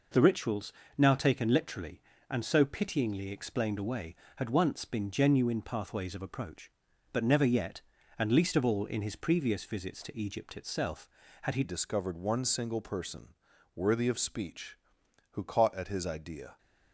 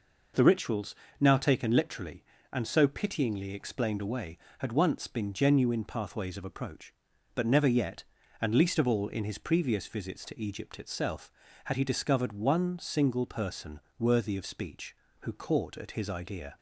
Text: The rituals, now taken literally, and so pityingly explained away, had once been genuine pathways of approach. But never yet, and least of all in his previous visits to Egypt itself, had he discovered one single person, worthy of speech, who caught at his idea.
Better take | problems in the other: second | changes voice at "discovered"; from 11.6 s on; 4.9 s long

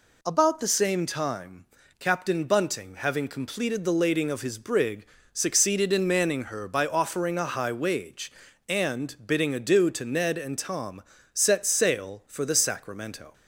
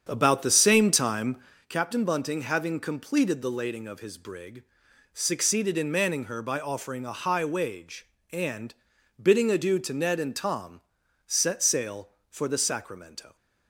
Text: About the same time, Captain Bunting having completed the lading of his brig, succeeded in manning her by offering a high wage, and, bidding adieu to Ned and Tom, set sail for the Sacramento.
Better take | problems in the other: first | starts louder than the rest; strong; until 1.6 s; 8 dB

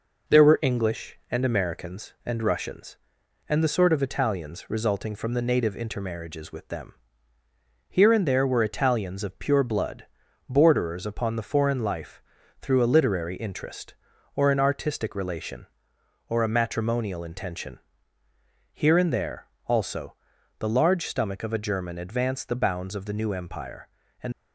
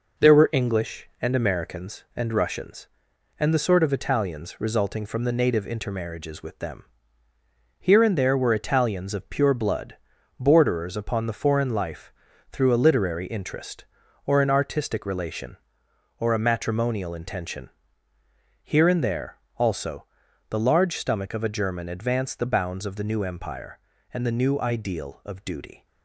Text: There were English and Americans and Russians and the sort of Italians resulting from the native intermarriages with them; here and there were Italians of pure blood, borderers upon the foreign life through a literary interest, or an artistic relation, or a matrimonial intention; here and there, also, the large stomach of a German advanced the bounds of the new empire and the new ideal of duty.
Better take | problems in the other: second | pauses between "life" and "through"; at 12.2 s; 0.40 s long; also in the second // stops before "the new ideal of duty"; at 24.3 s

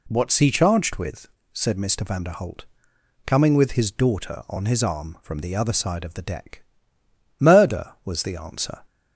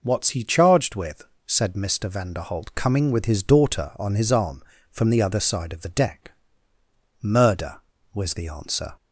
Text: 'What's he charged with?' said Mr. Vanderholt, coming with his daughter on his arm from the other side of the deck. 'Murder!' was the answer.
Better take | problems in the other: neither | none

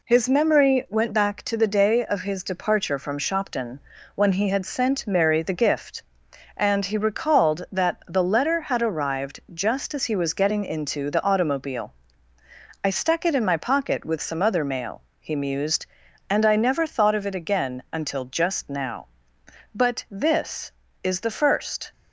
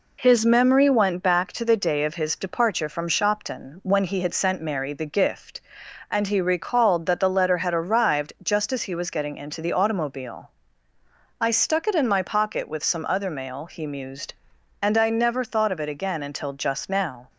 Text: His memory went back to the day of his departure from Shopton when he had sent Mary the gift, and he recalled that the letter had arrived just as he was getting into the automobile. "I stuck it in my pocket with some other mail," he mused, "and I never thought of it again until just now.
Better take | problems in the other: second | pauses between "Shopton" and "when"; at 3.7 s; 0.38 s long // pauses between "arrived" and "just"; slight; at 9.3 s; 0.16 s long // goes on to say "But this is the first"; strong; from 19.7 s on; 2.2 s long

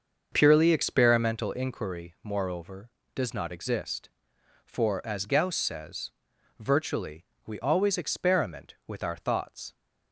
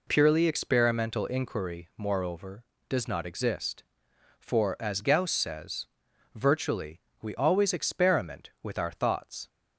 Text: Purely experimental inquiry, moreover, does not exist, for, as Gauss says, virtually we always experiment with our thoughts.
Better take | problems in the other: second | starts louder than the rest; until 1.4 s; 6.5 dB // pauses between "virtually" and "we"; slight; at 7.2 s; 0.20 s long; slight in the second

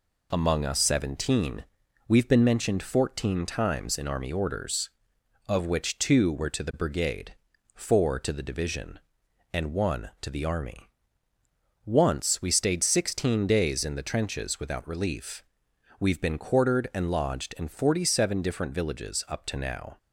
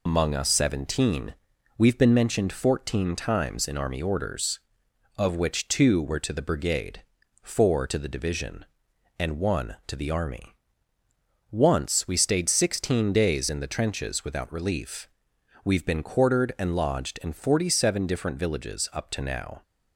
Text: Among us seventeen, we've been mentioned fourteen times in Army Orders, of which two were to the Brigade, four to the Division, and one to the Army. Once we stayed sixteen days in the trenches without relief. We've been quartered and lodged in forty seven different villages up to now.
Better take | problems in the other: first | loses the start of "Among"; at 0.0 s; 55 ms

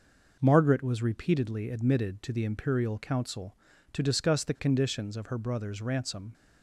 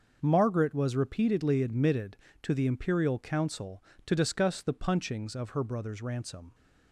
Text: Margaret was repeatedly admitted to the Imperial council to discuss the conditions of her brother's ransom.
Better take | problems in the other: first | starts louder than the rest; until 1.2 s; 6.5 dB // says "punchings" for "conditions"; at 4.7 s

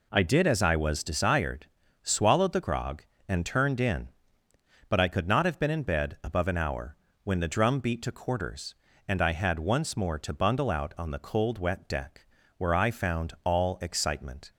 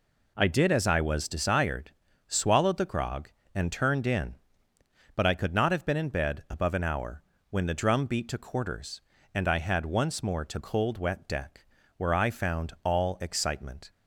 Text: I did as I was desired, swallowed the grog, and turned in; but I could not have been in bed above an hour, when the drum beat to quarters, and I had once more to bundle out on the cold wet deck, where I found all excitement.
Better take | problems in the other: first | skips "bundle out on the"; at 10.5 s

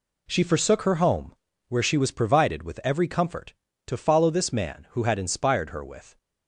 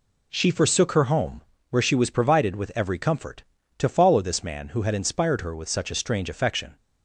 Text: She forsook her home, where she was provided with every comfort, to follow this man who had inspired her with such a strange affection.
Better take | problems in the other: second | stops before "such a strange affection"; at 6.1 s

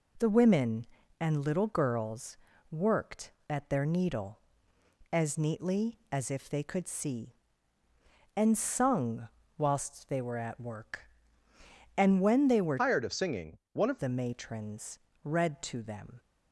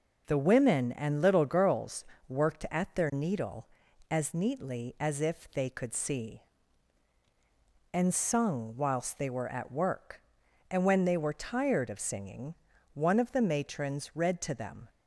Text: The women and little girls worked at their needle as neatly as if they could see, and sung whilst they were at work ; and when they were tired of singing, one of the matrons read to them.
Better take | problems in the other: second | pauses between "girls" and "worked"; slight; at 2.3 s; 0.32 s long; slight in the second // pauses between "sung" and "whilst"; slight; at 9.2 s; 0.30 s long // changes voice from "tired" to "of"; from 12.7 to 13.9 s; 1.2 s long // pauses between "matrons" and "read"; slight; at 14.9 s; 0.24 s long

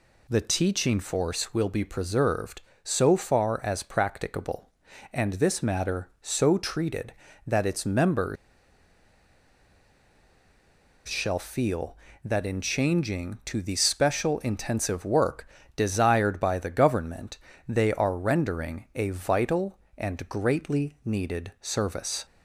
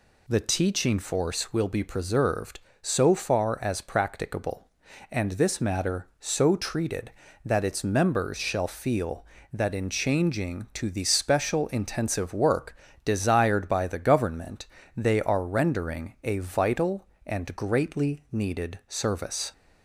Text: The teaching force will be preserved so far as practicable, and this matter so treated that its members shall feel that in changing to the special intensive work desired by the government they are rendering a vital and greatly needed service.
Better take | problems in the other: second | pauses between "members" and "shall"; strong; at 8.3 s; 2.7 s long // pauses between "work" and "desired"; slight; at 15.4 s; 0.28 s long; slight in the second // pauses between "government" and "they"; slight; at 17.3 s; 0.32 s long; slight in the second

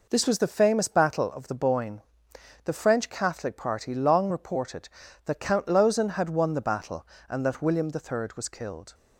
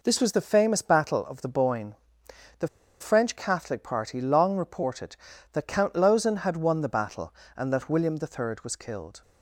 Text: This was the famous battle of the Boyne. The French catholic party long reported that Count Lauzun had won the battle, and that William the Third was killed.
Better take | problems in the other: first | pauses between "The" and "French"; slight; at 2.6 s; 0.33 s long

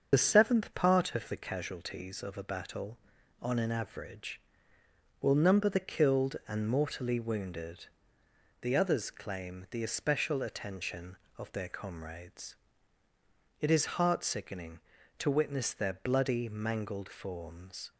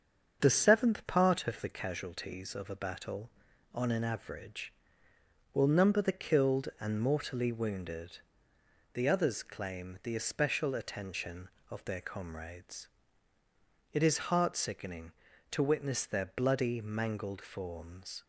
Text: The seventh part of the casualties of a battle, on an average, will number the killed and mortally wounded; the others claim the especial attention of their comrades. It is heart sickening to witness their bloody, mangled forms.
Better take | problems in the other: second | loses the start of "The"; at 0.1 s; 35 ms // starts louder than the rest; until 1.1 s; 7 dB; also in the second

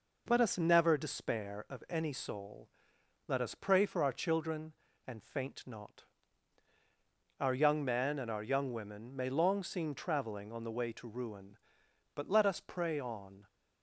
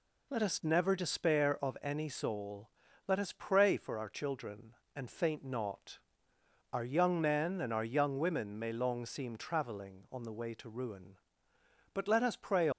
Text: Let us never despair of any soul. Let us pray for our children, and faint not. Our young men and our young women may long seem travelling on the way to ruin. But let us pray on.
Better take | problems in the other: first | stops before "on"; at 12.7 s

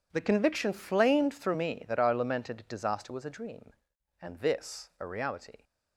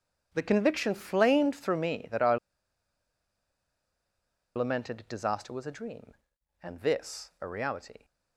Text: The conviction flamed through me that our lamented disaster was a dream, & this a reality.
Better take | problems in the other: first | pauses between "our" and "lamented"; strong; at 2.3 s; 2.1 s long

